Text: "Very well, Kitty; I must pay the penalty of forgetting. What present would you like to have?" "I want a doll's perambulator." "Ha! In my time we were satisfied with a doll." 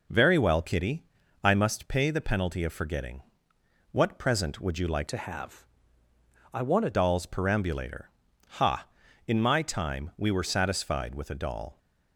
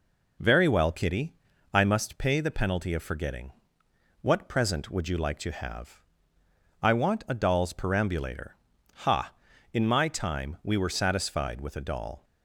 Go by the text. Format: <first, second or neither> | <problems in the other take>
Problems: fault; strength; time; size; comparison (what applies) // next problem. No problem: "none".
second | changes voice from "to" to "a"; from 5.0 to 6.9 s; 1.9 s long